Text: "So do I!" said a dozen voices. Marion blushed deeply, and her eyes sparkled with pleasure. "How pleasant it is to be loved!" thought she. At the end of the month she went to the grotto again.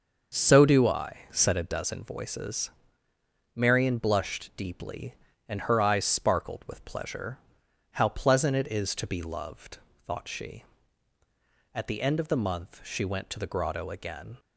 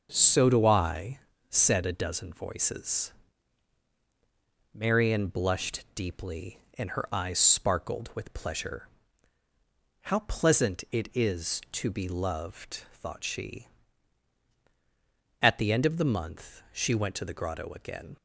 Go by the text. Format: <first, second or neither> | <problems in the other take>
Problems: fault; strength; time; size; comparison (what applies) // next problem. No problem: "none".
neither | starts louder than the rest; the same in both